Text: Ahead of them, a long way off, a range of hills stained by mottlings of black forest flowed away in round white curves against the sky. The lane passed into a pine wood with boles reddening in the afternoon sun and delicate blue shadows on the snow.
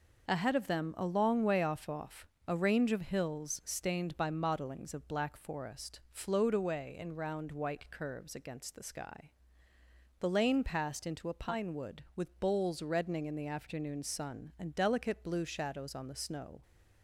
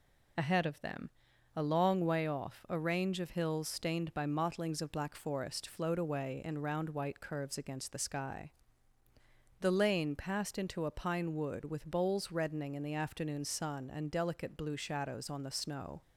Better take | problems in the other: second | says "off" twice; at 1.8 s

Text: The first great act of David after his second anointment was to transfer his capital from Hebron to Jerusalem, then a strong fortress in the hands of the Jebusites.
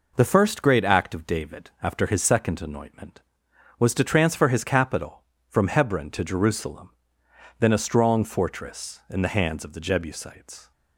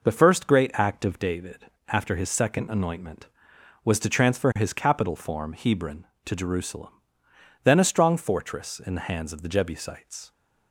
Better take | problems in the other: first | pauses between "David" and "after"; slight; at 1.6 s; 0.22 s long // says "form" for "from"; at 5.1 s

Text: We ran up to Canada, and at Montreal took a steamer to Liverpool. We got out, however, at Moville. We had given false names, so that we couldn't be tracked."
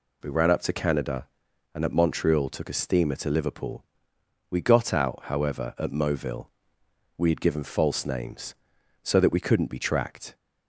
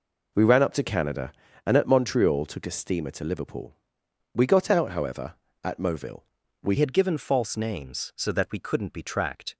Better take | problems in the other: first | changes voice at "had"; from 6.7 s on; 2.8 s long

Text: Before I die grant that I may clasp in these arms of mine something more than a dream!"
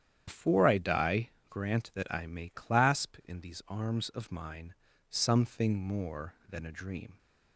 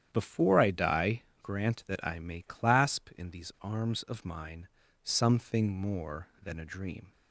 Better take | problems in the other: second | loses the start of "Before"; at 0.2 s; 70 ms // starts louder than the rest; strong; until 1.2 s; 9.5 dB; strong in the second // pauses between "die" and "grant"; slight; at 1.2 s; 0.20 s long; slight in the second // pauses between "mine" and "something"; slight; at 4.7 s; 0.36 s long; slight in the second

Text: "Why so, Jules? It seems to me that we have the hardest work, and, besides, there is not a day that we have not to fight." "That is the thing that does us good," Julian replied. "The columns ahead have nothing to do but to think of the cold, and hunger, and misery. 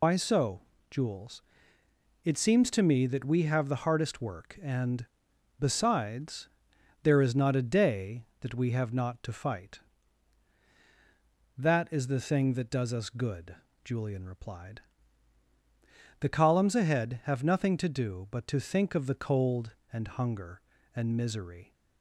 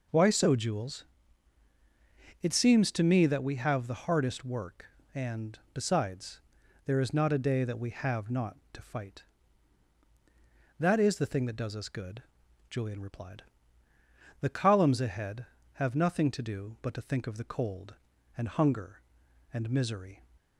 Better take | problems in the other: second | loses the start of "Why"; at 0.0 s; 90 ms

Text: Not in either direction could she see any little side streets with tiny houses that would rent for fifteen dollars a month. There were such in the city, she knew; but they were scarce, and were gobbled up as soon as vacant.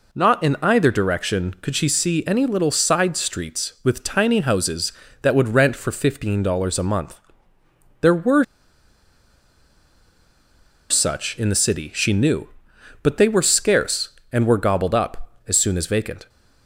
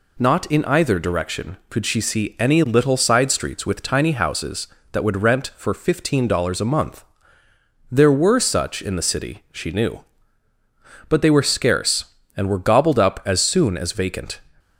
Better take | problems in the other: second | pauses between "were" and "such"; strong; at 8.4 s; 2.4 s long

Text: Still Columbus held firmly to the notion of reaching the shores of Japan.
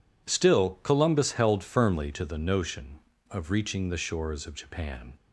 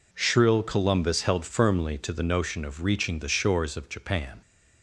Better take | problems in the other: first | says "Shrill" for "Still"; at 0.1 s

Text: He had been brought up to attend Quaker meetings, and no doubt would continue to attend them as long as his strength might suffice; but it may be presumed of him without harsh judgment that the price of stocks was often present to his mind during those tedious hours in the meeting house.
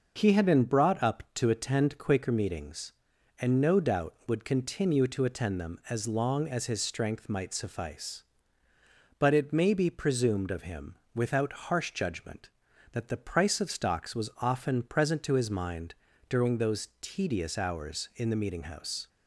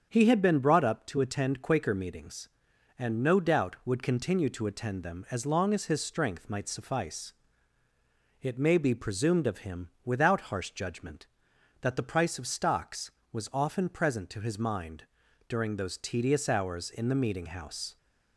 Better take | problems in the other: first | starts louder than the rest; strong; until 1.1 s; 7.5 dB // skips "but"; at 7.8 s // pauses between "him" and "without"; slight; at 9.8 s; 0.16 s long; slight in the first // pauses between "mind" and "during"; noticeable; at 15.0 s; 0.46 s long; slight in the first

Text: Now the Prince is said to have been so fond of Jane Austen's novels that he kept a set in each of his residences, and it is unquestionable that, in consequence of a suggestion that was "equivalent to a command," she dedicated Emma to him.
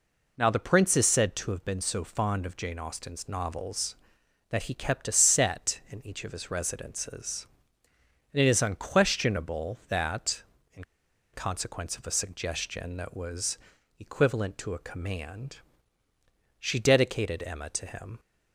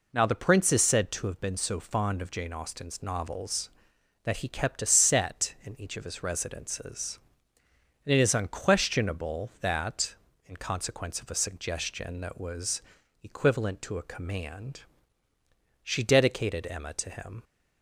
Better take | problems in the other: second | pauses between "in" and "consequence"; noticeable; at 10.8 s; 0.50 s long // pauses between "was" and "equivalent"; at 13.5 s; 0.42 s long; also in the second

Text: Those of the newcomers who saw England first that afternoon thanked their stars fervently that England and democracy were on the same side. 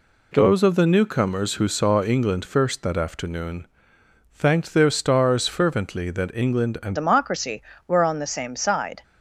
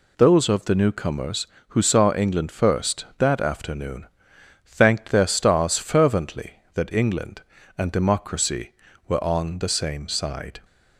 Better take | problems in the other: second | pauses between "afternoon" and "thanked"; noticeable; at 3.6 s; 0.66 s long; noticeable in the second // changes voice at "democracy"; from 6.9 s on; 2.1 s long

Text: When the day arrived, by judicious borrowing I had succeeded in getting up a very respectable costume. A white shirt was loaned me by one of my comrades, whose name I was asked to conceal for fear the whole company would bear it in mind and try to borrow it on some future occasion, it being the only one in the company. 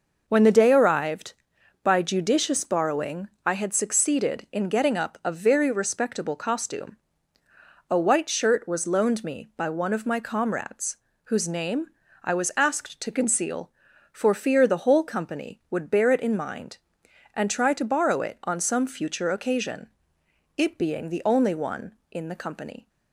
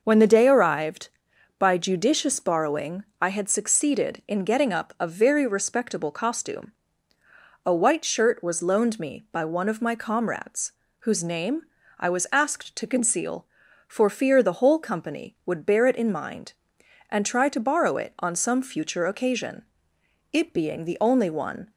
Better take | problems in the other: first | pauses between "borrowing" and "I"; slight; at 3.0 s; 0.16 s long; slight in the first // pauses between "name" and "I"; at 11.6 s; 0.38 s long; also in the first // stops before "in the company"; at 21.6 s

